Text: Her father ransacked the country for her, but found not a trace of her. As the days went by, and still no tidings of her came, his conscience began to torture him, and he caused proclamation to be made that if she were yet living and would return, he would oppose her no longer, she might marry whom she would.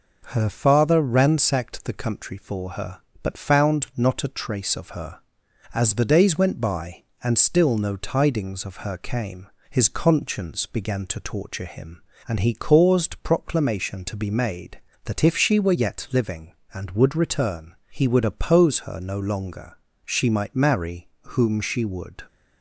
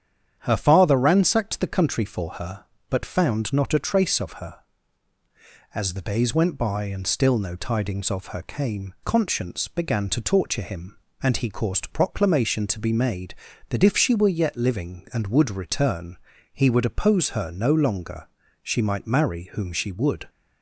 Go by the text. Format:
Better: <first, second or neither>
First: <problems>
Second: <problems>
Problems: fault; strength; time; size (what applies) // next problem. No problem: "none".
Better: first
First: none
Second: starts louder than the rest; strong; until 1.4 s; 9 dB // skips "his"; at 8.9 s